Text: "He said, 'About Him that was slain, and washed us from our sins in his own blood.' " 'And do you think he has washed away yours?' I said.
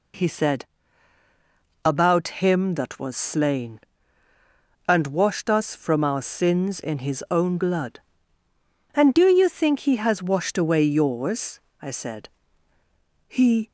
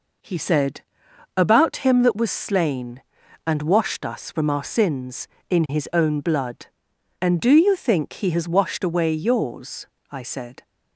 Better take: second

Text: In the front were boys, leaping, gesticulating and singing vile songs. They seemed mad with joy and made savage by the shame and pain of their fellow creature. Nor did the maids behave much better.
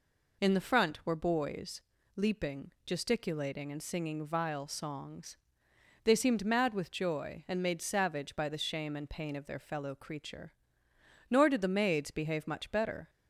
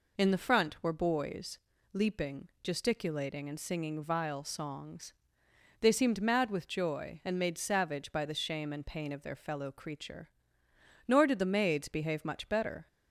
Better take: neither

